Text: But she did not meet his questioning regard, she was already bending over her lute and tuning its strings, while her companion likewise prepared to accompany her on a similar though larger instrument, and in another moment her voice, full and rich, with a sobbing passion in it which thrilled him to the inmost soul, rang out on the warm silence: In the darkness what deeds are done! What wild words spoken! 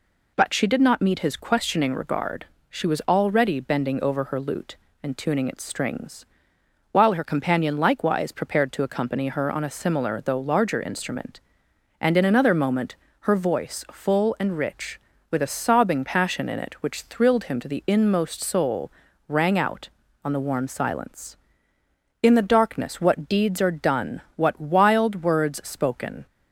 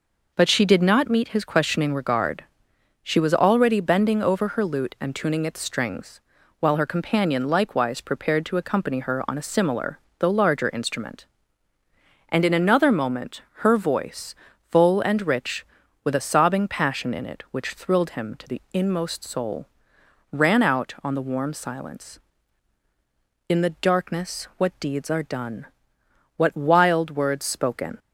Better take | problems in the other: first | pauses between "similar" and "though"; slight; at 9.9 s; 0.20 s long // pauses between "moment" and "her"; slight; at 13.4 s; 0.16 s long; slight in the first // says "ran" for "rang"; at 20.3 s

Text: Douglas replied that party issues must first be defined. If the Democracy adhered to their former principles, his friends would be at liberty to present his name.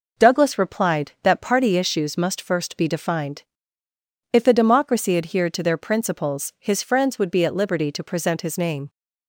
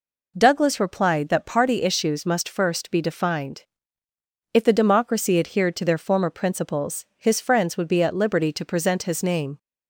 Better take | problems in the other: second | skips "former"; at 5.7 s

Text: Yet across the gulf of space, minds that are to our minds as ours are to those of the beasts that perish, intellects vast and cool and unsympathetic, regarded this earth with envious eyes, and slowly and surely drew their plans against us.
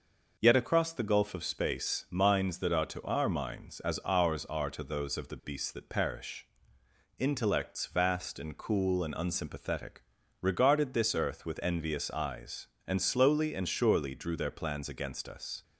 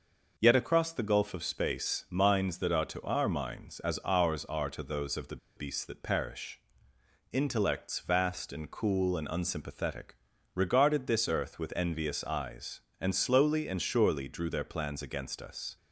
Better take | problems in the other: first | pauses between "the" and "beasts"; slight; at 5.3 s; 0.19 s long

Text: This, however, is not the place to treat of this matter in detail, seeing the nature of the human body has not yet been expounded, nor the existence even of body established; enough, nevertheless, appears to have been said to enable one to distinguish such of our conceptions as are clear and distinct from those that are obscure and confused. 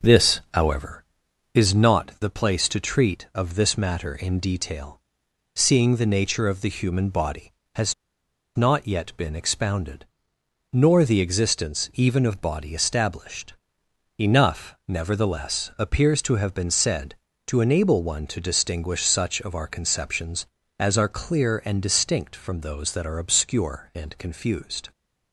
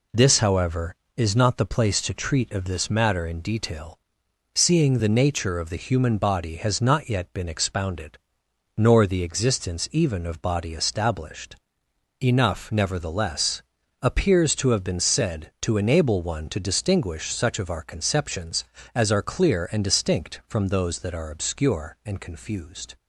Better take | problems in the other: second | pauses between "has" and "not"; noticeable; at 7.9 s; 0.61 s long

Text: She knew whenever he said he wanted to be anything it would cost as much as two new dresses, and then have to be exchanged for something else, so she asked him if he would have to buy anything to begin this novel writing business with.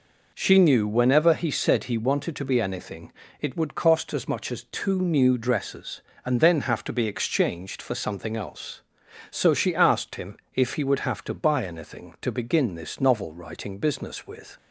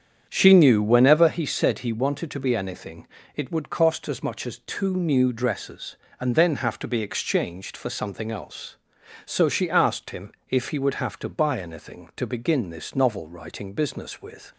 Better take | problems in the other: first | starts louder than the rest; strong; until 1.4 s; 8.5 dB // pauses between "anything" and "it"; slight; at 3.0 s; 0.26 s long; slight in the first // pauses between "him" and "if"; slight; at 10.3 s; 0.18 s long; slight in the first

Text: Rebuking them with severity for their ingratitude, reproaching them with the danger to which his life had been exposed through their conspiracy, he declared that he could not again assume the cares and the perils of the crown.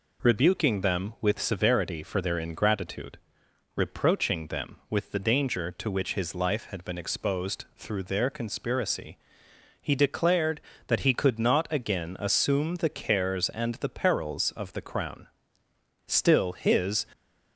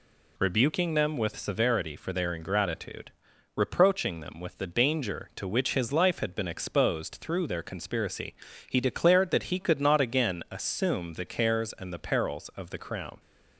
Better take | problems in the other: second | goes on to say "Still his"; noticeable; from 16.0 s on; 1.0 s long

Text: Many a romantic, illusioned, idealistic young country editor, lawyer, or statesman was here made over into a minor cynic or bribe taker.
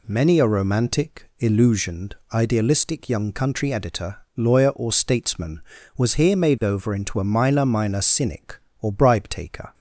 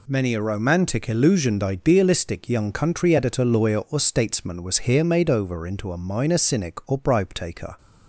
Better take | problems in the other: second | says "minor" twice; at 7.6 s

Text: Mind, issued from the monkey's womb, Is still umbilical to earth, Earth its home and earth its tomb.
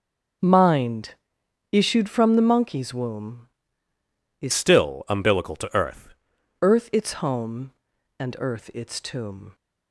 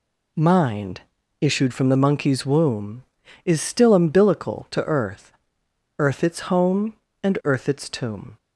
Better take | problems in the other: second | starts louder than the rest; until 1.9 s; 6.5 dB // changes voice from "still" to "earth"; from 4.5 to 6.0 s; 1.5 s long

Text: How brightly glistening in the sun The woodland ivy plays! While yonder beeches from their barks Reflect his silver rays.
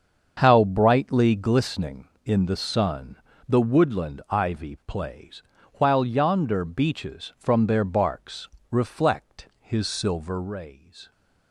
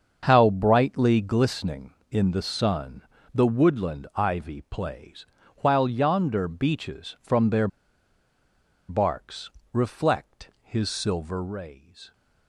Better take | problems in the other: first | starts louder than the rest; until 1.3 s; 7 dB; also in the first // pauses between "sun" and "The"; slight; at 3.0 s; 0.32 s long; slight in the first // pauses between "their" and "barks"; at 7.6 s; 1.2 s long // pauses between "barks" and "Reflect"; slight; at 9.5 s; 0.22 s long; slight in the first

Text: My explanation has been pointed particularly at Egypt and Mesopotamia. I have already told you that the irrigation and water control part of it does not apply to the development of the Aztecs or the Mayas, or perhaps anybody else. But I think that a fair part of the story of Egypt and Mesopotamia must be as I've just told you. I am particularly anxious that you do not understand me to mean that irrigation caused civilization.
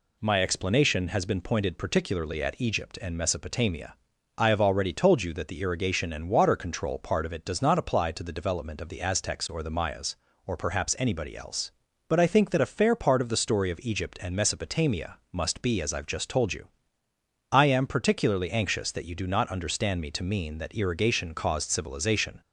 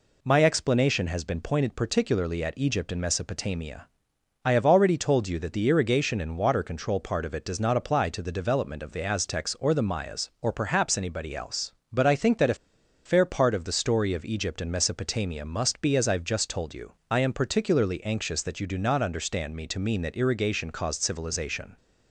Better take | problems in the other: first | pauses between "a" and "fair"; noticeable; at 12.5 s; 0.50 s long

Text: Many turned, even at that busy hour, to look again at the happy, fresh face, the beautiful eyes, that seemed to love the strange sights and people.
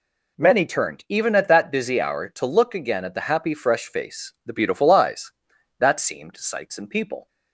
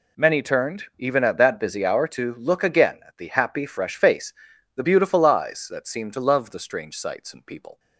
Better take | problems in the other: second | skips "to love the strange"; at 6.3 s

